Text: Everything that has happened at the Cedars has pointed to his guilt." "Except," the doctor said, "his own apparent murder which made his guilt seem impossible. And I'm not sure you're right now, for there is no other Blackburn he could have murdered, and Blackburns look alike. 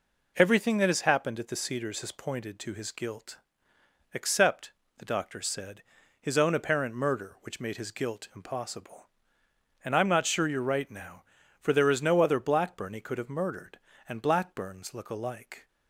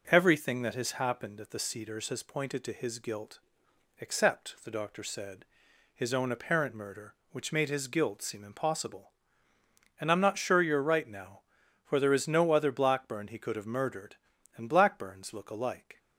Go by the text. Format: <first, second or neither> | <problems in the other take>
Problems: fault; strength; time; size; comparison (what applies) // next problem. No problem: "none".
second | skips "seem"; at 8.3 s